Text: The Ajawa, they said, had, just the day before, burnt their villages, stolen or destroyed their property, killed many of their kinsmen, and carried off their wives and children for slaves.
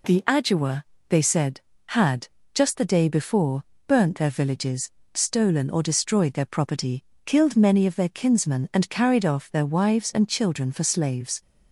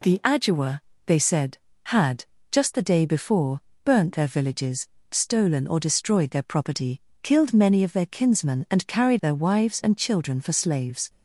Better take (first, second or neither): first